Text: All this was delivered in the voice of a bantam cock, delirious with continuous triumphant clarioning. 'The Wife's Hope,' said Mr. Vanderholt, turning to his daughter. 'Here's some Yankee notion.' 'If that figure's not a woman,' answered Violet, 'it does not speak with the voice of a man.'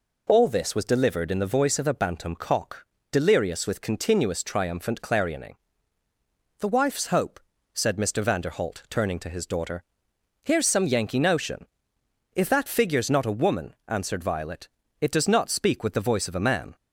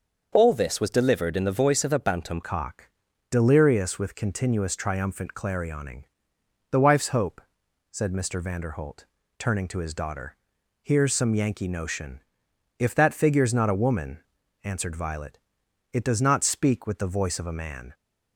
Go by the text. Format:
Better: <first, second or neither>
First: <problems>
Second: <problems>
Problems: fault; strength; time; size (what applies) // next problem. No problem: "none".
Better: first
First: none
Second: starts louder than the rest; until 1.3 s; 6.5 dB // changes voice at "cock"; from 2.4 s on; 15.5 s long